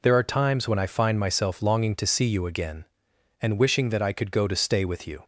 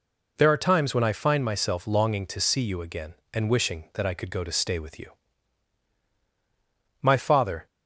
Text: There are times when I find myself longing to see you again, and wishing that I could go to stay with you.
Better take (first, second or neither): first